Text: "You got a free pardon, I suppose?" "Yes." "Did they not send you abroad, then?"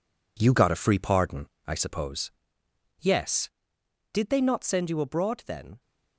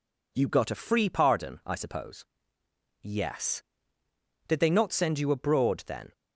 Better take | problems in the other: second | gets quieter; strong; throughout; 7.5 dB

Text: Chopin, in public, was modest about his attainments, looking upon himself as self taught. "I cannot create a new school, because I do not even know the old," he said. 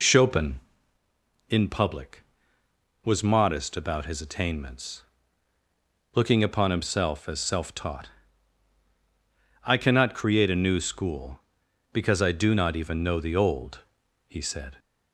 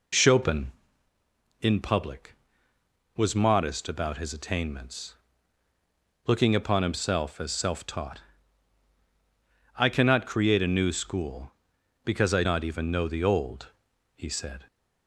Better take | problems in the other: first | skips "do"; at 12.4 s

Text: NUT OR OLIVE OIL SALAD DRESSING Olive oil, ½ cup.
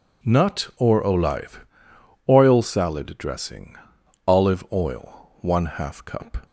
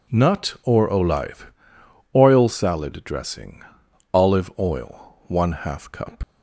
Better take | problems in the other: first | pauses between "OLIVE" and "OIL"; noticeable; at 1.5 s; 0.64 s long; noticeable in the first // pauses between "DRESSING" and "Olive"; noticeable; at 3.6 s; 0.52 s long; noticeable in the first // leaves "cup" unfinished; at 6.2 s; 85 ms

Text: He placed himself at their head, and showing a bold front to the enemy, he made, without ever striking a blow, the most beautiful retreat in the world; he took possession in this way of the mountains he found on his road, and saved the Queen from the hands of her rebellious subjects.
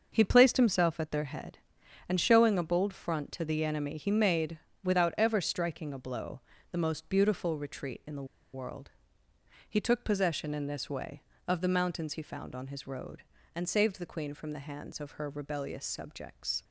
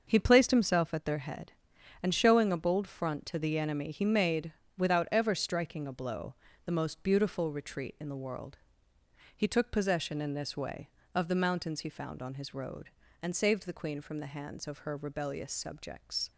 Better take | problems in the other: second | starts louder than the rest; until 1.1 s; 6 dB; also in the second // pauses between "the" and "world"; slight; at 8.2 s; 0.28 s long

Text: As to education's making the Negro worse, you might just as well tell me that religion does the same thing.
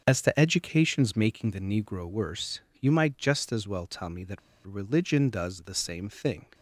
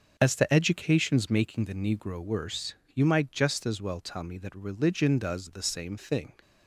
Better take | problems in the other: second | starts louder than the rest; until 1.0 s; 6.5 dB; also in the second // pauses between "that" and "religion"; slight; at 4.3 s; 0.26 s long

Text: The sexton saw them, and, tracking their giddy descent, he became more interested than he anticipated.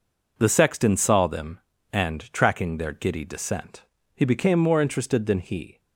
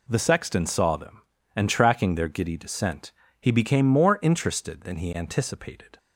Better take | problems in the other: second | stops before "anticipated"; at 5.7 s

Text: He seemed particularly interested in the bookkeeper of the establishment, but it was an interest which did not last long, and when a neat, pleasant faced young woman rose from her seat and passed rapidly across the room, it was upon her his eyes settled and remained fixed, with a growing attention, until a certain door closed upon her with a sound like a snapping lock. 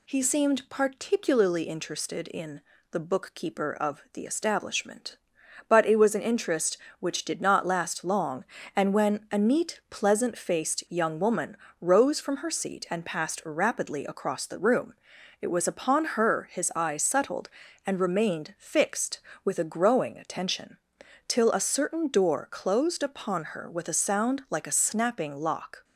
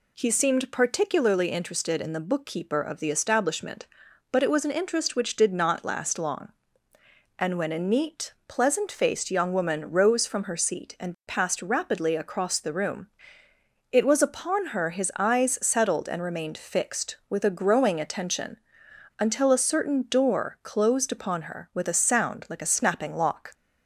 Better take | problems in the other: second | pauses between "in" and "the"; slight; at 2.6 s; 0.30 s long // pauses between "woman" and "rose"; slight; at 11.5 s; 0.24 s long // says "till" for "until"; at 21.2 s

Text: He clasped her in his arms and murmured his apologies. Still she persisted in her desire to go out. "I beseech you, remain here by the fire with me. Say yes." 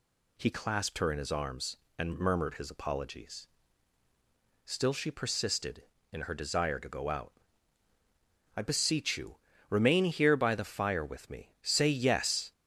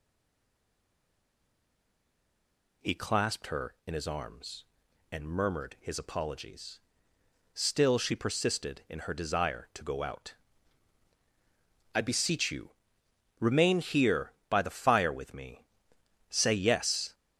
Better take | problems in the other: first | stays silent before the first word; strong; until 2.8 s; 2.8 s long

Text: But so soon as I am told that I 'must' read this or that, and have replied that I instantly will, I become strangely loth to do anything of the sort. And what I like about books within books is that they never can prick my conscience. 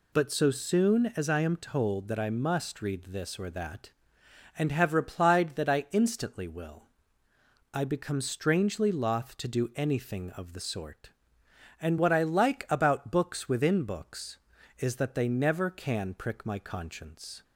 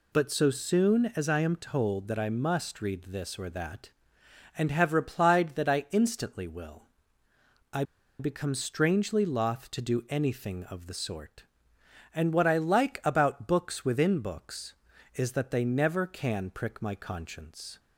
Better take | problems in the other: first | pauses between "I" and "become"; at 7.8 s; 0.36 s long

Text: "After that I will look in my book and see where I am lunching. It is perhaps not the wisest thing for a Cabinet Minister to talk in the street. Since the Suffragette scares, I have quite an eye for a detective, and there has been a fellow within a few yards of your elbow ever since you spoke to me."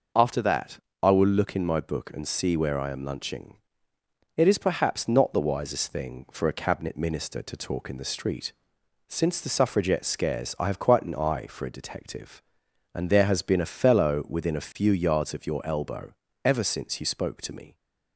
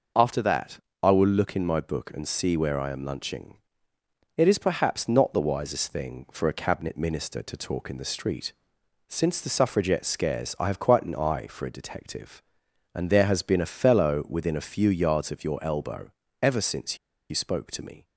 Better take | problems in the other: first | pauses between "that" and "I"; slight; at 0.7 s; 0.22 s long; slight in the first // pauses between "elbow" and "ever"; slight; at 16.0 s; 0.32 s long; slight in the first // pauses between "since" and "you"; slight; at 16.9 s; 0.32 s long

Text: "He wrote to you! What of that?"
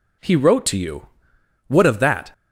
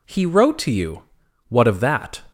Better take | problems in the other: neither | none

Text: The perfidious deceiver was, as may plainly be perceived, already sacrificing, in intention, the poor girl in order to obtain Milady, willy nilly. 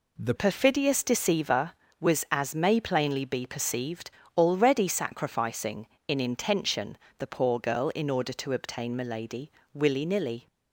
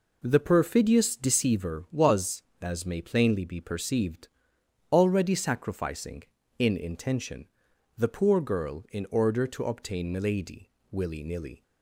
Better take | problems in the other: second | changes voice at "perfidious"; from 0.3 s on; 10.1 s long

